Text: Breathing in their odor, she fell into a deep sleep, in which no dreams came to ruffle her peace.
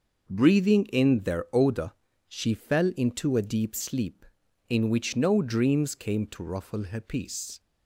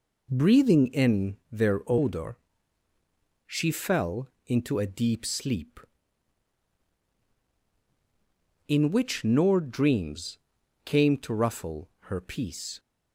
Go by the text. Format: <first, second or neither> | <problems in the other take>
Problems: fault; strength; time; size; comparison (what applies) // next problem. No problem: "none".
first | pauses between "fell" and "into"; slight; at 4.2 s; 0.18 s long // says "nor" for "no"; at 9.2 s // pauses between "dreams" and "came"; noticeable; at 10.3 s; 0.48 s long